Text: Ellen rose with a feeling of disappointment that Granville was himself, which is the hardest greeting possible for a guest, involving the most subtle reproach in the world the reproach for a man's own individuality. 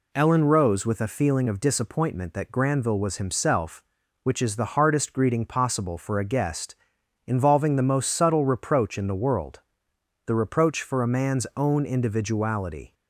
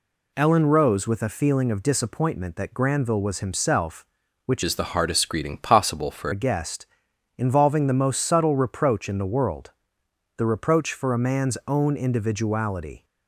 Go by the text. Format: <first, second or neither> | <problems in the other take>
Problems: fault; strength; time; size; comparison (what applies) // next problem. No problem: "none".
first | changes voice from "is" to "for"; from 4.6 to 6.3 s; 1.7 s long // pauses between "world" and "the"; noticeable; at 9.7 s; 0.66 s long; noticeable in the first